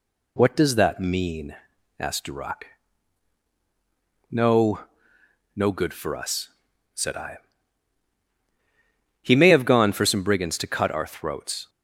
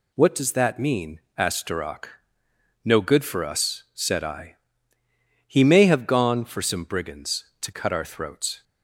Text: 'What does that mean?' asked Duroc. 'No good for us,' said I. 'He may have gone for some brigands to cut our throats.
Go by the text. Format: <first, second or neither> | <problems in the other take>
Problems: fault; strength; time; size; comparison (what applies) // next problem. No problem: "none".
second | says "No" twice; at 5.5 s